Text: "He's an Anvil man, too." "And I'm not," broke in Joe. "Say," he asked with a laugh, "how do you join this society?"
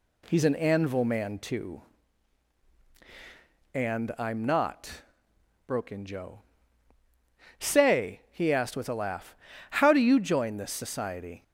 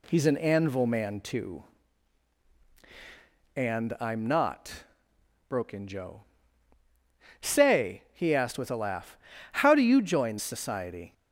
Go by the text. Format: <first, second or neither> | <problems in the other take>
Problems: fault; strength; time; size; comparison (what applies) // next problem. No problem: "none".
first | skips "this"; at 10.4 s